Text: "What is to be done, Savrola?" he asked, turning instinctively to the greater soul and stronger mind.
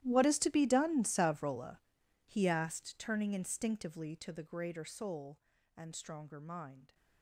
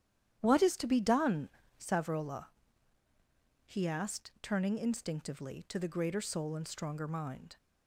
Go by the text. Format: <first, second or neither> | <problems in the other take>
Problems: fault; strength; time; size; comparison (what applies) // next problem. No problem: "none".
second | gets quieter; strong; throughout; 20.5 dB // starts louder than the rest; strong; until 1.0 s; 13 dB; strong in the second